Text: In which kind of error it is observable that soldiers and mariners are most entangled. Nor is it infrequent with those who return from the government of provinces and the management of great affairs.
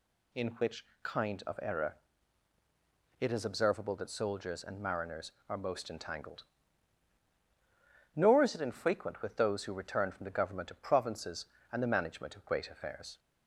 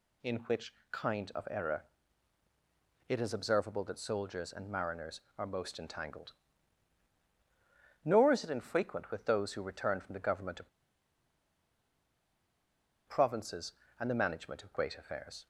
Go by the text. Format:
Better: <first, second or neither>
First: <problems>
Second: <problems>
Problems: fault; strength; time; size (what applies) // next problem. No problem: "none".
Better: first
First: pauses between "which" and "kind"; slight; at 0.8 s; 0.18 s long // pauses between "error" and "it"; at 1.9 s; 1.2 s long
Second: pauses between "which" and "kind"; slight; at 0.7 s; 0.18 s long // pauses between "error" and "it"; at 1.8 s; 1.2 s long // pauses between "of" and "provinces"; strong; at 10.6 s; 2.3 s long